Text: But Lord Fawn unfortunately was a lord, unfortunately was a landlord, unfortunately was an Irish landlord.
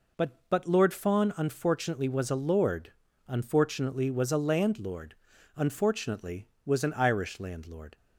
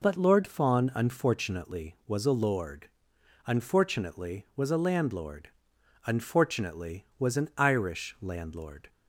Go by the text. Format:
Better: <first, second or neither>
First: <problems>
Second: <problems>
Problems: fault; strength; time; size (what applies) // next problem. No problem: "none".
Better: second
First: says "But" twice; at 0.4 s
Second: none